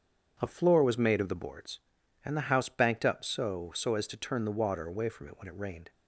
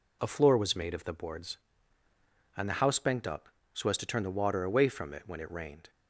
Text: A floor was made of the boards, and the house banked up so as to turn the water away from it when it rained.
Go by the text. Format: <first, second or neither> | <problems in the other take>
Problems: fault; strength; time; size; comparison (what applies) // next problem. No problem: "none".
second | starts louder than the rest; strong; until 1.4 s; 7.5 dB // says "so" twice; at 3.7 s